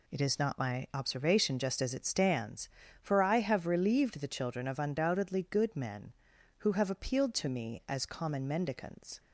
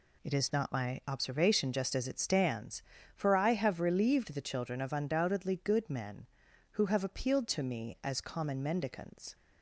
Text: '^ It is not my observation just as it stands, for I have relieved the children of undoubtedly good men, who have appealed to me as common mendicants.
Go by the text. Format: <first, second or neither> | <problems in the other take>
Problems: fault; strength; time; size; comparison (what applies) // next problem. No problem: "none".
neither | none